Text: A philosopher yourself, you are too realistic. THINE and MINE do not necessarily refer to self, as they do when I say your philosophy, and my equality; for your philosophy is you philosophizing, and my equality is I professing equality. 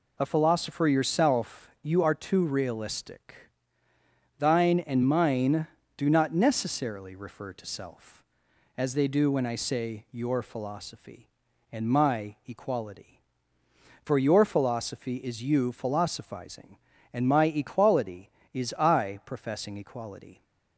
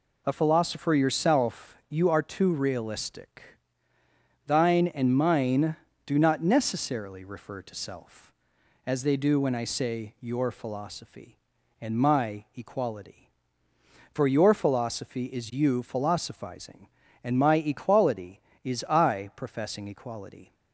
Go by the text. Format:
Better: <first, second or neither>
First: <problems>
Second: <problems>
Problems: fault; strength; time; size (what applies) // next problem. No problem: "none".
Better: neither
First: none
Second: none